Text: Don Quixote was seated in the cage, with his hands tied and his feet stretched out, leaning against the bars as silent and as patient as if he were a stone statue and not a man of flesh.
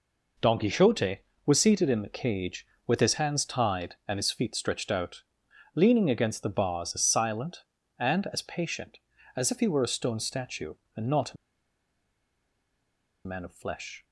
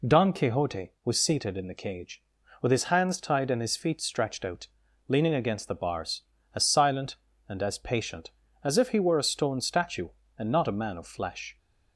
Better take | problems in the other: second | pauses between "a" and "man"; strong; at 11.3 s; 1.9 s long

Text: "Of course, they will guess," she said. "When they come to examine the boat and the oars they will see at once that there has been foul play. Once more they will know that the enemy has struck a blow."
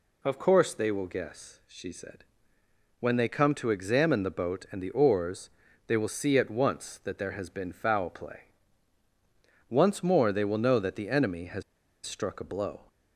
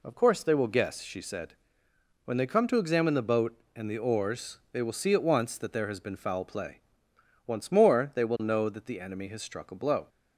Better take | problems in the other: second | pauses between "oars" and "they"; at 5.4 s; 0.38 s long // pauses between "has" and "struck"; at 11.6 s; 0.43 s long

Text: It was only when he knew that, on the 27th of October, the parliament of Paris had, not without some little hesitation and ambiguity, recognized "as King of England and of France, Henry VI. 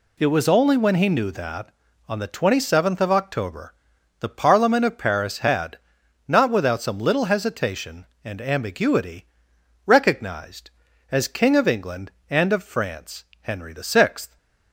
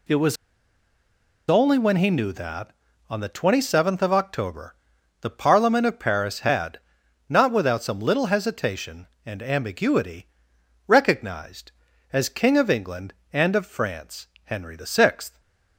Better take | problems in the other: first | pauses between "was" and "only"; at 0.3 s; 1.1 s long

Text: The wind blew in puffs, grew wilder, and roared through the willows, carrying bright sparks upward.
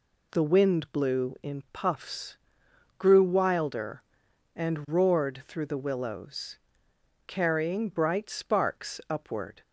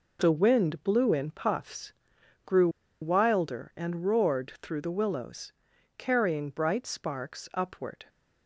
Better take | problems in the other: first | pauses between "grew" and "wilder"; slight; at 2.6 s; 0.33 s long

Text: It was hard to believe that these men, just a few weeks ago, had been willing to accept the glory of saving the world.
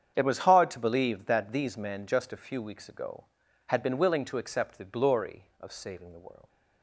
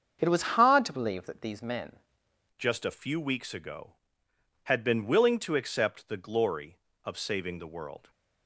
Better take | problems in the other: first | starts louder than the rest; until 1.2 s; 7 dB; strong in the first // changes voice at "just"; from 2.5 s on; 5.5 s long

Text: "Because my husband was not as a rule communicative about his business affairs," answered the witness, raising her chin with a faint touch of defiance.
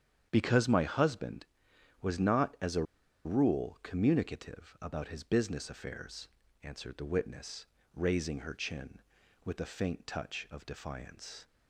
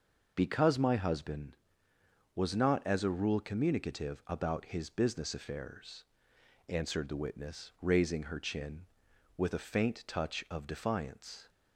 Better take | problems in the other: second | starts louder than the rest; strong; until 1.3 s; 8.5 dB // pauses between "a" and "rule"; at 2.8 s; 0.42 s long

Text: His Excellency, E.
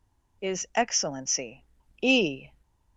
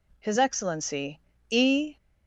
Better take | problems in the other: second | says "Is" for "His"; at 0.4 s

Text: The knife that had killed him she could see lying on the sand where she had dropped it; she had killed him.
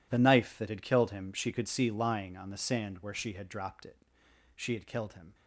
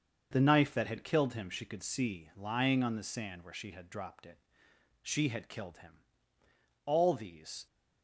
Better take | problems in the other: first | starts louder than the rest; until 1.3 s; 6.5 dB // goes on to say "All these"; noticeable; from 6.8 s on; 0.80 s long

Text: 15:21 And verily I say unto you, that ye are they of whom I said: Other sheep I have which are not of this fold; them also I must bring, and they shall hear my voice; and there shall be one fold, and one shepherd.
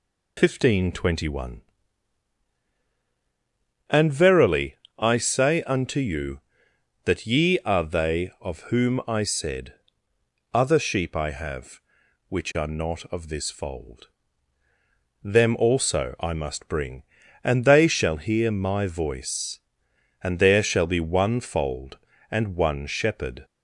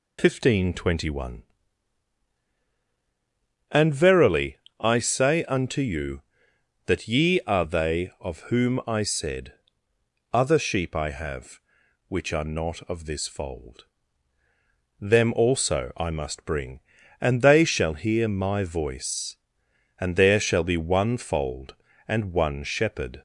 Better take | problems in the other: neither | pauses between "verily" and "I"; slight; the same in both

